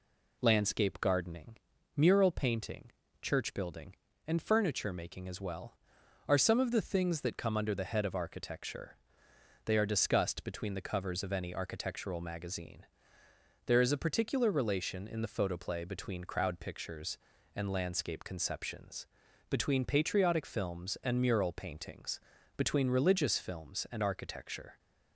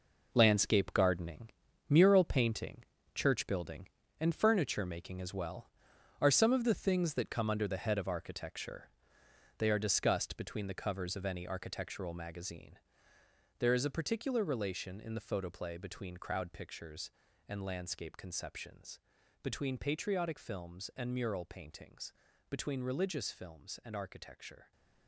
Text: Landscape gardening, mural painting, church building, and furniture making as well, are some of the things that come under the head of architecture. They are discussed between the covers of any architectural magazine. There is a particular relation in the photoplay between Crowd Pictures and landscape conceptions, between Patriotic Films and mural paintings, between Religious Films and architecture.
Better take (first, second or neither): first